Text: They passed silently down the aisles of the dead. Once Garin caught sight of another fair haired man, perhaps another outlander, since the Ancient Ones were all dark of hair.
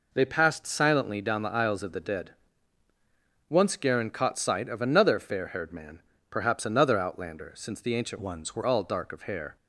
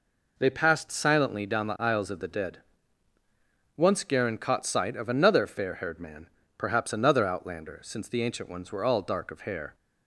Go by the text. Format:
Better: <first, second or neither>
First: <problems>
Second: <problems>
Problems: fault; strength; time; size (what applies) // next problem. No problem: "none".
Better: second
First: changes voice from "Ones" to "were"; from 8.1 to 8.6 s; 0.5 s long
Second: none